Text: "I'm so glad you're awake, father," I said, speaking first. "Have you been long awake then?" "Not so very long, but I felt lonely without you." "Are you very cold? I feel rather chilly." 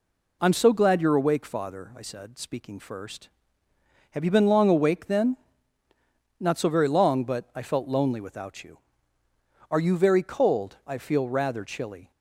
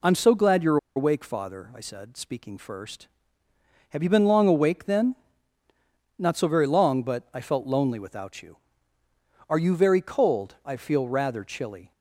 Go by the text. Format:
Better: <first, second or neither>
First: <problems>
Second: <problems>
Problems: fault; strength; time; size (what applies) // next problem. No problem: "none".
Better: first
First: none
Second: pauses between "you're" and "awake"; slight; at 0.7 s; 0.19 s long